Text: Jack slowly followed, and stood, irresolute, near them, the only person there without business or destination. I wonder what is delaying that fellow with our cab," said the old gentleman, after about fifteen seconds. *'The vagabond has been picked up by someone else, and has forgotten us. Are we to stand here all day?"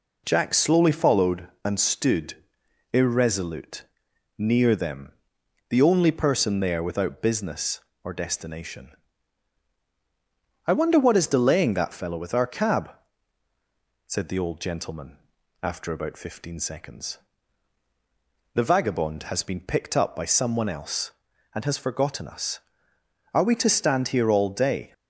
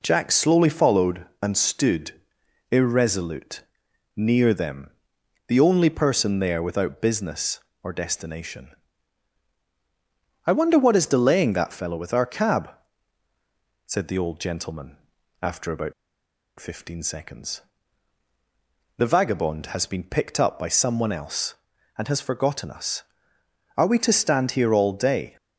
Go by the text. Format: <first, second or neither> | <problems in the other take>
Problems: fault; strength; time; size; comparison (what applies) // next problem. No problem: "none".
first | pauses between "about" and "fifteen"; noticeable; at 15.9 s; 0.66 s long